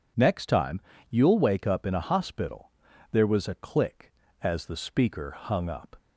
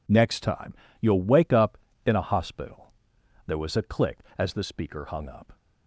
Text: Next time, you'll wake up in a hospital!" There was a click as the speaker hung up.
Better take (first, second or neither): neither